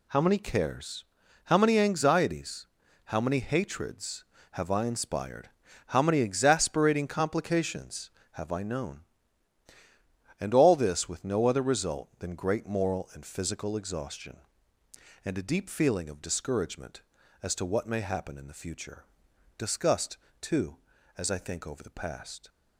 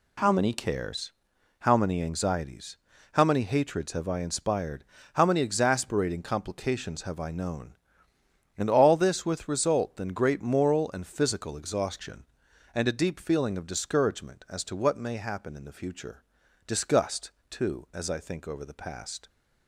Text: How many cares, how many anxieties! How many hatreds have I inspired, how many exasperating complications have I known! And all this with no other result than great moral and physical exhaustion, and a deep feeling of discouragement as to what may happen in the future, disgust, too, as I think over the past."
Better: first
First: none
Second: skips "no other"; at 9.4 s

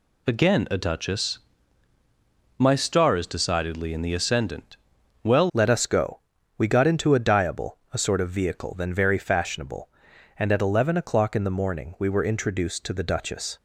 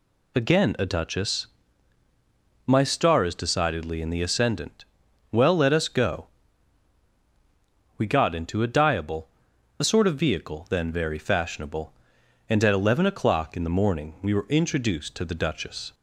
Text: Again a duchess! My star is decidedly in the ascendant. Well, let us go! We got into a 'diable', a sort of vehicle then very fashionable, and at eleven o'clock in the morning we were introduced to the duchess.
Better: second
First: changes voice at "let"; from 5.5 s on; 8.0 s long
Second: none

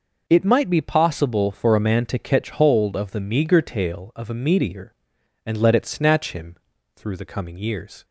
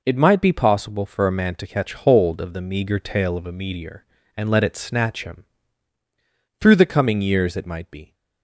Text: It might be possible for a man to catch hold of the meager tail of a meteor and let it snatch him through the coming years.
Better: first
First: pauses between "him" and "through"; at 6.5 s; 0.38 s long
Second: pauses between "him" and "through"; at 5.4 s; 1.1 s long // goes on to say "It might be"; from 7.5 s on; 0.58 s long

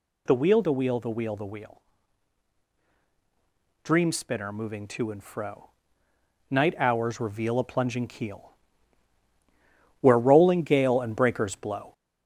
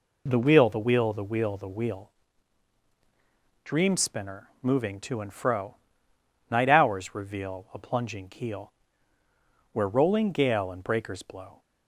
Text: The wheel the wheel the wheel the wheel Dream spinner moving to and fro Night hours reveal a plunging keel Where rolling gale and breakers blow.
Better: second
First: gets louder; slight; throughout; 3.5 dB // pauses between "wheel" and "Dream"; strong; at 1.8 s; 2.0 s long // pauses between "fro" and "Night"; noticeable; at 5.7 s; 0.80 s long // pauses between "keel" and "Where"; strong; at 8.5 s; 1.5 s long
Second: pauses between "wheel" and "Dream"; strong; at 2.1 s; 1.5 s long // pauses between "fro" and "Night"; noticeable; at 5.7 s; 0.74 s long // pauses between "keel" and "Where"; noticeable; at 8.7 s; 0.98 s long

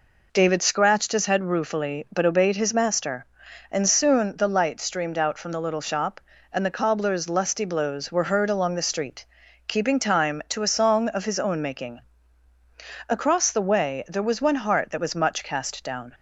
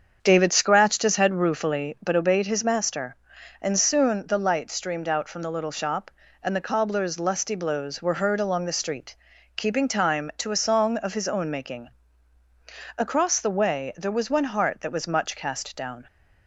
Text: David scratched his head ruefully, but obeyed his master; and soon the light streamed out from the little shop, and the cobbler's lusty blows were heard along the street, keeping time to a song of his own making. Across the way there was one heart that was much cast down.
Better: first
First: none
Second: starts louder than the rest; until 2.0 s; 7 dB

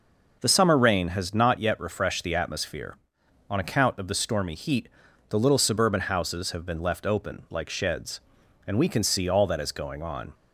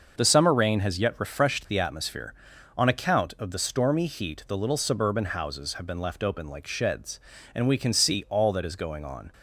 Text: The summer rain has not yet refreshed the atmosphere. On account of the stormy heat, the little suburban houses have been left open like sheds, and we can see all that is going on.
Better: first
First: none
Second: starts louder than the rest; noticeable; until 1.1 s; 6 dB // skips "not"; at 0.9 s

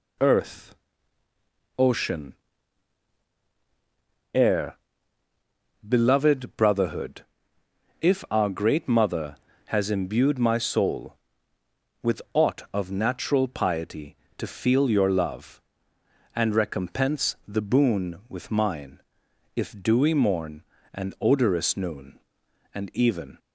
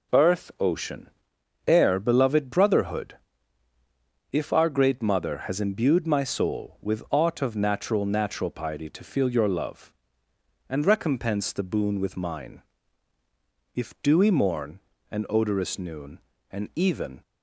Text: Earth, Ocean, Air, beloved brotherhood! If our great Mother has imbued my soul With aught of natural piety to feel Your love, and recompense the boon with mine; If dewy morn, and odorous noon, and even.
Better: first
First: none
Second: says "natural" twice; at 8.0 s

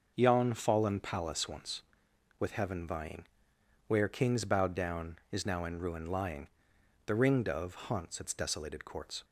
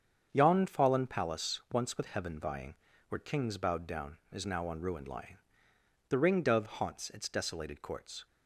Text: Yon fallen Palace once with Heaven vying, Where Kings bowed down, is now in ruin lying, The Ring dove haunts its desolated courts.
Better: first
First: starts louder than the rest; noticeable; until 1.1 s; 6 dB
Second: starts louder than the rest; strong; until 1.3 s; 7.5 dB // says "on" for "in"; at 4.6 s

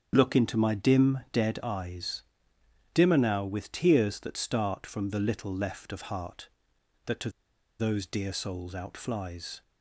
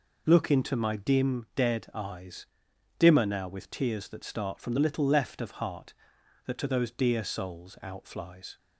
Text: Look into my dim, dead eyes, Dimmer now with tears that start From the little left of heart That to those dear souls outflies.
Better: second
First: starts louder than the rest; strong; until 1.1 s; 8 dB // pauses between "to" and "those"; noticeable; at 7.3 s; 0.49 s long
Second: none

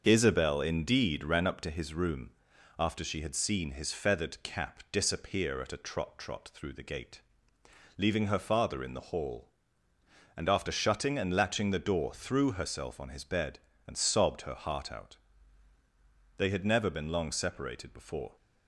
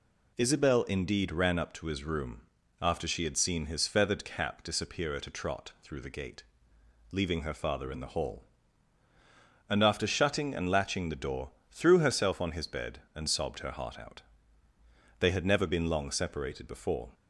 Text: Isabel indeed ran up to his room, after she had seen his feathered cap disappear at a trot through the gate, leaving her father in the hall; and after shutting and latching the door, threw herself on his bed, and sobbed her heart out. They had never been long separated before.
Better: second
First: starts louder than the rest; until 1.0 s; 6.5 dB // says "trot" twice; at 6.1 s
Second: none

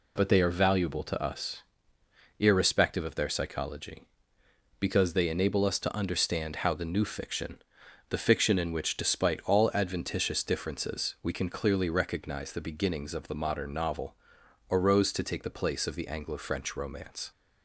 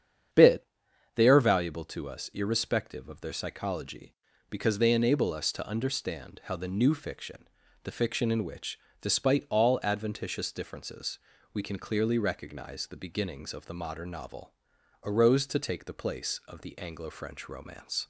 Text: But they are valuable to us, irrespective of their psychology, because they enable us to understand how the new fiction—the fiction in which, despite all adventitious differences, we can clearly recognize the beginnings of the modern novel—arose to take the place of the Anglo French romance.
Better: first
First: none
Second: starts louder than the rest; strong; until 1.8 s; 8 dB // says "Bit" for "But"; at 0.3 s

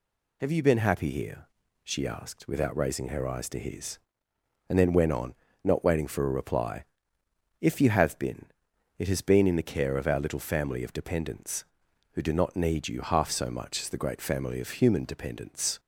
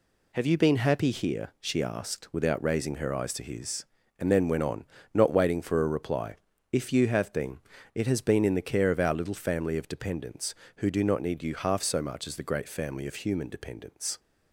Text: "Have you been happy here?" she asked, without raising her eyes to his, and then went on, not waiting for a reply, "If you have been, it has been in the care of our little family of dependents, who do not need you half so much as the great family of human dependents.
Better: neither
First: none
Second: none

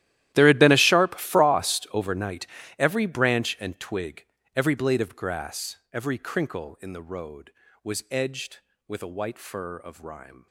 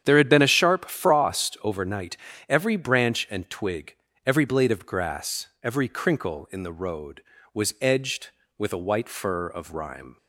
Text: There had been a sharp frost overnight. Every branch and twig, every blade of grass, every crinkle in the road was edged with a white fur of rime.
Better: second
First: gets quieter; strong; throughout; 19 dB // starts louder than the rest; strong; until 1.3 s; 13.5 dB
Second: starts louder than the rest; strong; until 1.0 s; 8.5 dB

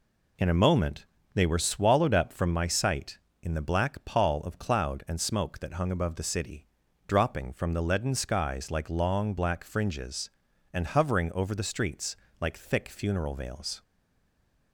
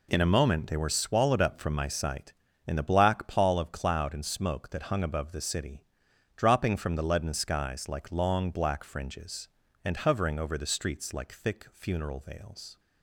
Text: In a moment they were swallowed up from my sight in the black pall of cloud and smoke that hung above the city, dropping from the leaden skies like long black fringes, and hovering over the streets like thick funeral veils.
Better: second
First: pauses between "moment" and "they"; slight; at 1.0 s; 0.28 s long // pauses between "streets" and "like"; slight; at 12.1 s; 0.24 s long // stays silent after the last word; slight; from 13.8 s on; 0.9 s long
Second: none

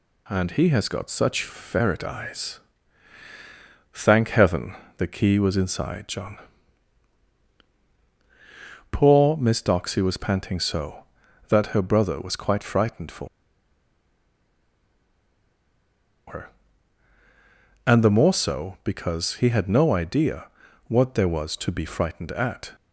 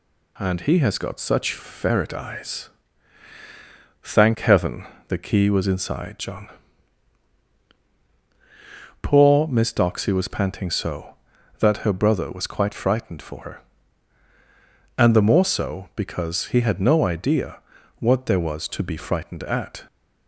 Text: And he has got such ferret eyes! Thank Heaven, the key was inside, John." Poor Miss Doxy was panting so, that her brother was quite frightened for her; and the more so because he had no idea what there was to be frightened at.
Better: second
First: pauses between "for" and "her"; strong; at 13.2 s; 3.0 s long // pauses between "idea" and "what"; at 20.4 s; 0.40 s long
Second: pauses between "idea" and "what"; at 17.5 s; 0.40 s long

